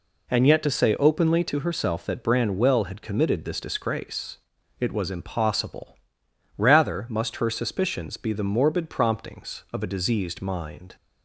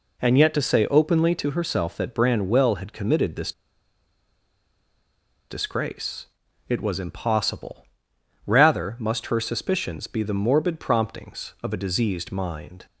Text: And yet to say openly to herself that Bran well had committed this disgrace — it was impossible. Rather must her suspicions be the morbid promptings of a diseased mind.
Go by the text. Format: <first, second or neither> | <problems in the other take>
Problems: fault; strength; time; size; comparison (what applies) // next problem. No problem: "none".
first | pauses between "this" and "disgrace"; strong; at 3.5 s; 1.9 s long